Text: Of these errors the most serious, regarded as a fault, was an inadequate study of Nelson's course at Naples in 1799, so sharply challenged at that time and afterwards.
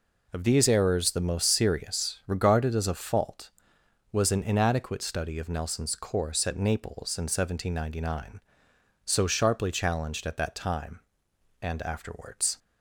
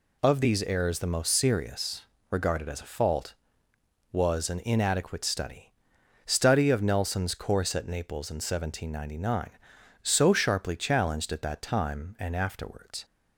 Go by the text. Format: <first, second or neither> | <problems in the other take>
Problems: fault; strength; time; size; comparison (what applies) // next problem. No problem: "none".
first | says "study" twice; at 6.2 s